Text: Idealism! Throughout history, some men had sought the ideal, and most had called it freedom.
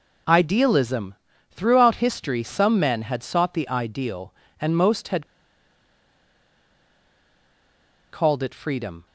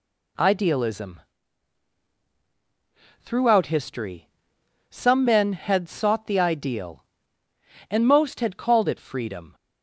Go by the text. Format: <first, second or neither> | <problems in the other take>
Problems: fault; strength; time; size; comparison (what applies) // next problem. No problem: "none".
second | pauses between "had" and "called"; strong; at 5.2 s; 2.8 s long